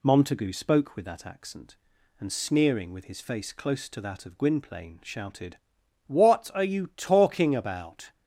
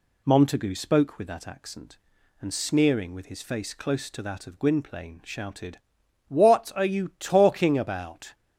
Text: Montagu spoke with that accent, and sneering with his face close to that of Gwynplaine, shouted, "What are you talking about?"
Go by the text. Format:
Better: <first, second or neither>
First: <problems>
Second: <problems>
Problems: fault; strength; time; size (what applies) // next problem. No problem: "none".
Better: neither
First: none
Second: none